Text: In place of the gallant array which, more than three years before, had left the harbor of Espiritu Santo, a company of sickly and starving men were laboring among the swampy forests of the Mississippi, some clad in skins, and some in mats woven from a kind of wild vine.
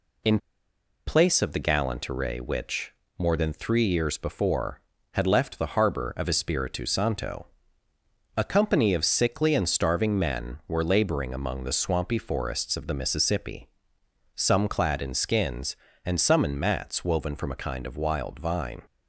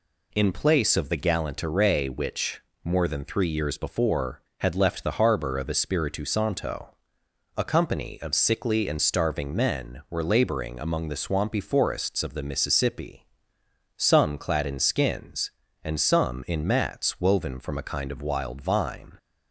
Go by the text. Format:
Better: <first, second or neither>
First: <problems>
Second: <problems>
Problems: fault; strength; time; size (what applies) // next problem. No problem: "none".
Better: second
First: pauses between "In" and "place"; noticeable; at 0.3 s; 0.69 s long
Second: none